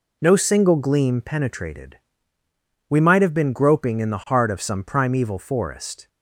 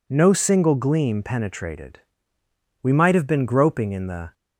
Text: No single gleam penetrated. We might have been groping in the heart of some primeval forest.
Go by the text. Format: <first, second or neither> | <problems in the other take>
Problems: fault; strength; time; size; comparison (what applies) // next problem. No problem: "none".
first | stops before "heart of some primeval forest"; at 4.3 s